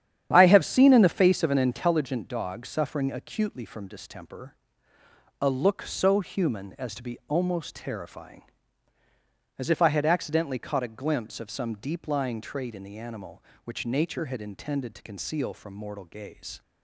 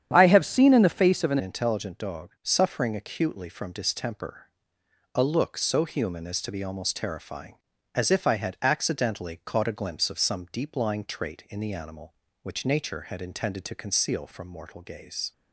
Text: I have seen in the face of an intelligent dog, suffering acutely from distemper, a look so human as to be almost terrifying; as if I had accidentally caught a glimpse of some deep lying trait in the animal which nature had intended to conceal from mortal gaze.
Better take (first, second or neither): first